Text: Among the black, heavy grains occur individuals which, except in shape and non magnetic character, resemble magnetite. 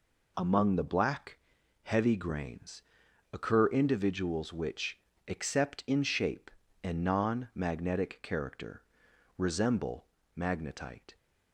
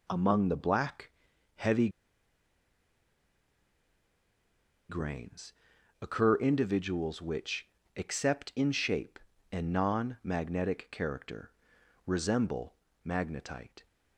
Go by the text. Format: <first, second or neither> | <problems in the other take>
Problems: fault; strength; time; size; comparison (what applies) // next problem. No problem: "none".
first | pauses between "heavy" and "grains"; strong; at 1.8 s; 3.0 s long // pauses between "grains" and "occur"; noticeable; at 5.5 s; 0.48 s long; noticeable in the first // pauses between "resemble" and "magnetite"; slight; at 12.7 s; 0.32 s long; slight in the first